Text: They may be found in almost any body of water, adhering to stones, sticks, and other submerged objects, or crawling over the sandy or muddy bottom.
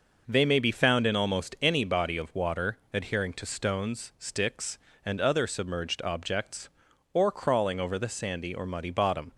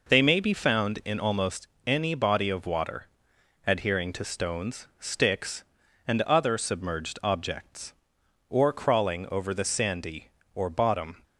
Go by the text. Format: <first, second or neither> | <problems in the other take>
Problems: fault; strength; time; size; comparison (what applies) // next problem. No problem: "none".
first | pauses between "almost" and "any"; slight; at 1.6 s; 0.18 s long // skips "muddy"; at 10.6 s